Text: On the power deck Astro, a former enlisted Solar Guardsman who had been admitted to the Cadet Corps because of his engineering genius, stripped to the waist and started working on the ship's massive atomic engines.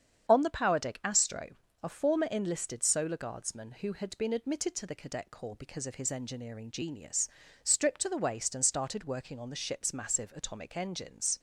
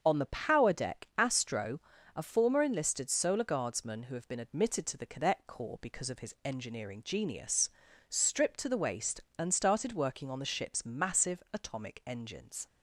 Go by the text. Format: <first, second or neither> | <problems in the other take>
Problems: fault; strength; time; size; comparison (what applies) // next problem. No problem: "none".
first | starts louder than the rest; until 1.0 s; 6.5 dB; strong in the first // says "have" for "had"; at 4.1 s